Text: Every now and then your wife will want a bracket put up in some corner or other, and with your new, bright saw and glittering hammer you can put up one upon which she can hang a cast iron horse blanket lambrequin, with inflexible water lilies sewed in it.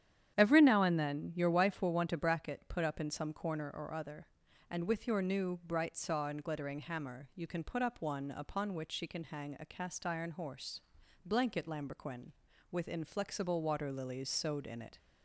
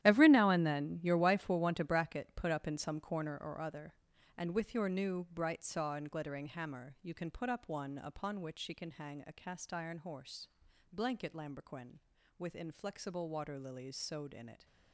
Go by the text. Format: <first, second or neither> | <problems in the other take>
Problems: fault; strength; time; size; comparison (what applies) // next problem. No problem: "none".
first | gets quieter; strong; throughout; 13.5 dB // starts louder than the rest; strong; until 1.0 s; 12.5 dB; strong in the first // pauses between "horse" and "blanket"; at 10.4 s; 0.44 s long; also in the first